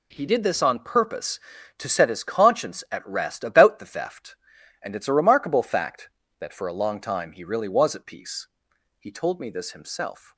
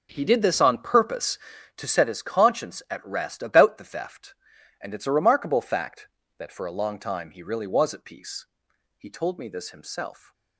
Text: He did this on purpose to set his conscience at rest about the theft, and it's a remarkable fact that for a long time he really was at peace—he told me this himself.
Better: first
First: none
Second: starts louder than the rest; noticeable; until 1.6 s; 5.5 dB

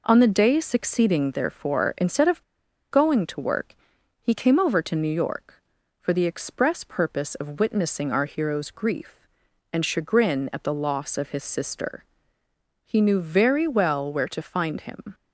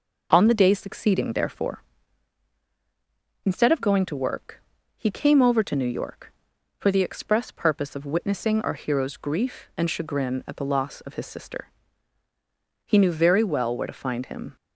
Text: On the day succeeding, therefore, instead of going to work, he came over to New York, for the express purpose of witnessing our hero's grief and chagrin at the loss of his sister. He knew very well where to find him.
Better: second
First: pauses between "of" and "going"; noticeable; at 2.4 s; 0.48 s long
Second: none

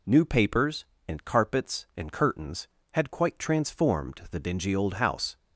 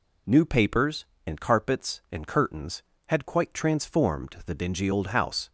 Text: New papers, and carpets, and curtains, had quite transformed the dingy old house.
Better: neither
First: none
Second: none

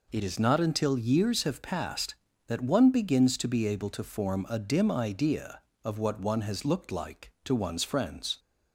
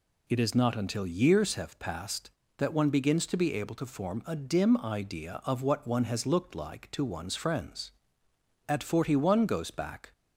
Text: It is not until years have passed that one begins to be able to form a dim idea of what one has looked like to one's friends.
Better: first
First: none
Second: goes on to say "At forty one goes back"; from 8.6 s on; 1.4 s long

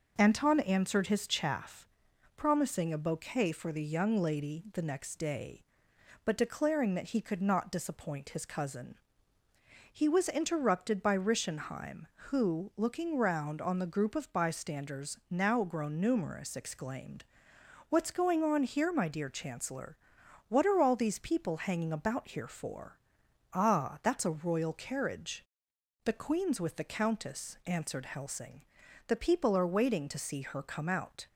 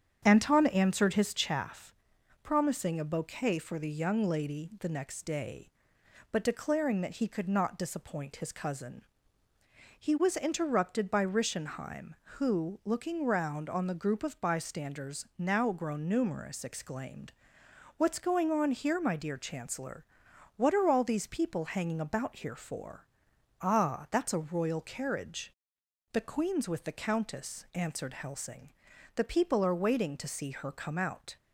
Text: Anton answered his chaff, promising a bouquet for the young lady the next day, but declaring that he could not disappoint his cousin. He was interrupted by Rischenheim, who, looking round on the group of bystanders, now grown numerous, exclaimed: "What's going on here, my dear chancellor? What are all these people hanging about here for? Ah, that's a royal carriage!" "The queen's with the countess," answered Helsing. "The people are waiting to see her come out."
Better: first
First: none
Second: starts louder than the rest; strong; until 1.5 s; 8 dB

